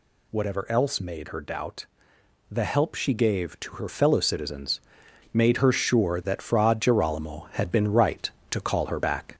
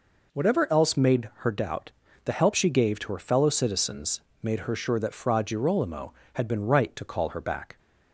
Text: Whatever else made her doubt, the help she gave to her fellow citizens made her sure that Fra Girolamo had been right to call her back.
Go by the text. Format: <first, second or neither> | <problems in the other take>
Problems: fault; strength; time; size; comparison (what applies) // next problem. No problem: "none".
second | gets louder; slight; throughout; 3 dB // pauses between "citizens" and "made"; noticeable; at 4.7 s; 0.54 s long; slight in the second